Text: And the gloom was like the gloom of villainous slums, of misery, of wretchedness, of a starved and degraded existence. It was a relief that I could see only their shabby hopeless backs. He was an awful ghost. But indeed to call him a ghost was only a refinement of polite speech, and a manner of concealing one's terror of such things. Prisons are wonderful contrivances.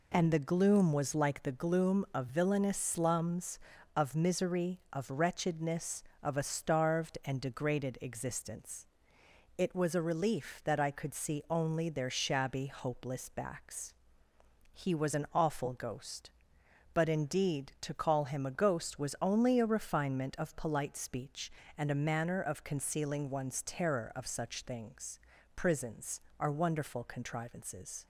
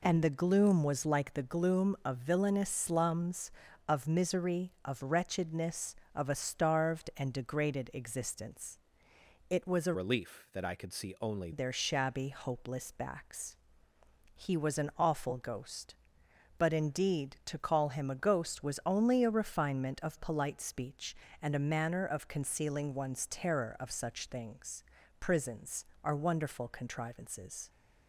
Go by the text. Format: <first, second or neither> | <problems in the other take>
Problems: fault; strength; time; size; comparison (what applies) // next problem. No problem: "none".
first | changes voice from "relief" to "only"; from 9.9 to 11.5 s; 1.6 s long